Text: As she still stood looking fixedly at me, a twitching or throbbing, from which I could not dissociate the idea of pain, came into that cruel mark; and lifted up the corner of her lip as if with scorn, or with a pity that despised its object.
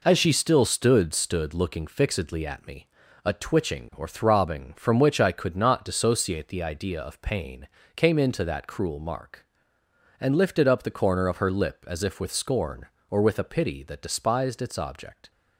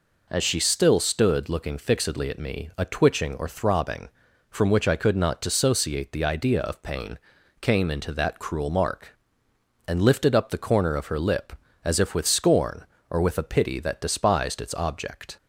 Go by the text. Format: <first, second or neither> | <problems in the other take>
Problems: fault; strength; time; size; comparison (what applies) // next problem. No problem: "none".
second | says "stood" twice; at 1.1 s